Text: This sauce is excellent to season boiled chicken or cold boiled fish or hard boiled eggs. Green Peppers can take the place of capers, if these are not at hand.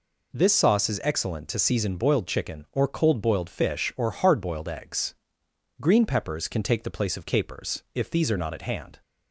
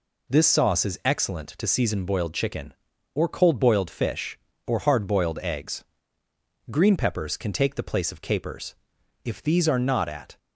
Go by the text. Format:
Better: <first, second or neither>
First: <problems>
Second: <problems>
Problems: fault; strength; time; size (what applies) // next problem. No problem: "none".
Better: first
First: none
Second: stops before "hand"; at 10.3 s